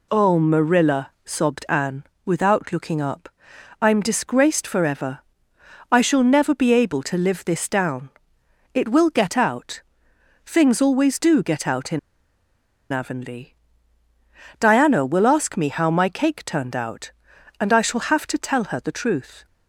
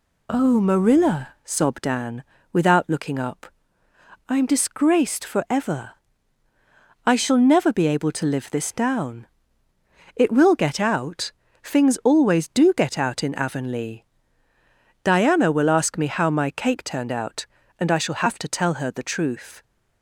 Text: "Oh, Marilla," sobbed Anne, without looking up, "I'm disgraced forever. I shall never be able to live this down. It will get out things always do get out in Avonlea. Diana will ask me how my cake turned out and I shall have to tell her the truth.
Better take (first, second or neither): second